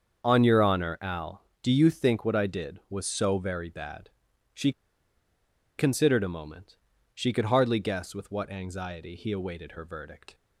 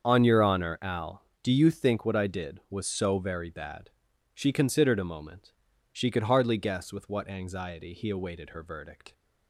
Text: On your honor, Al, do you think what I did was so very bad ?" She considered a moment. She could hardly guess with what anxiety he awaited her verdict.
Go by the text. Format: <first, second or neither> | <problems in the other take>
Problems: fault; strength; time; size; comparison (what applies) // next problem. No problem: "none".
second | starts louder than the rest; until 1.2 s; 7 dB; also in the second // pauses between "She" and "considered"; at 4.7 s; 1.0 s long